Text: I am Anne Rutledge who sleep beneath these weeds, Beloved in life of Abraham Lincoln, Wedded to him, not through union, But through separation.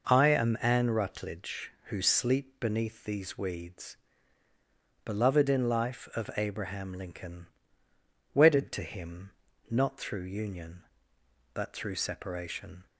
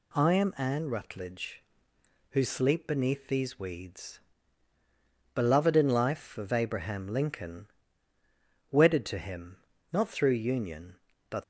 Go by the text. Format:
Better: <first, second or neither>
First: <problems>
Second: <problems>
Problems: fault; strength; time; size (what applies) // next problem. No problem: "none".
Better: first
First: none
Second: stops before "through separation"; at 11.4 s